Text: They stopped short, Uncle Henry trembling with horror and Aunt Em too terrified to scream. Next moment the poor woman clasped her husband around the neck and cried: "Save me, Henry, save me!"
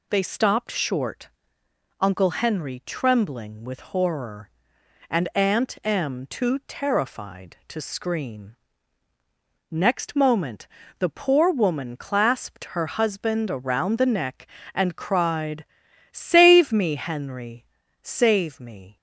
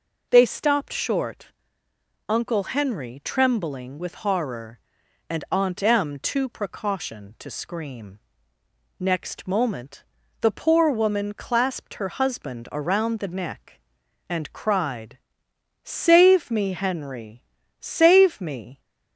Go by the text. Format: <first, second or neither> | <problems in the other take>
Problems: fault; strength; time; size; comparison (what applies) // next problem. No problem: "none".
first | says "precaution" for "terrified"; at 6.4 s // pauses between "moment" and "the"; at 10.0 s; 0.38 s long; slight in the first